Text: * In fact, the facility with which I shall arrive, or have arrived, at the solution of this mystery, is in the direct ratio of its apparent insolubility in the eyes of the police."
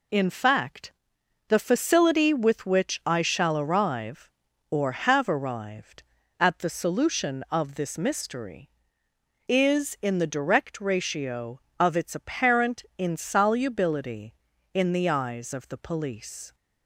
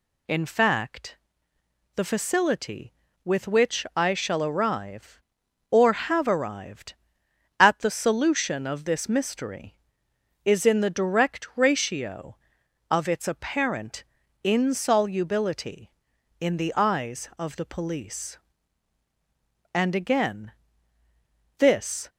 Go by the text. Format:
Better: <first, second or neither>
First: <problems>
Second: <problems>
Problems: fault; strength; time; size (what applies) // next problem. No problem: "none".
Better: first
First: none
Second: pauses between "apparent" and "insolubility"; at 14.0 s; 0.40 s long // goes on to say "And again This"; strong; from 19.7 s on; 2.3 s long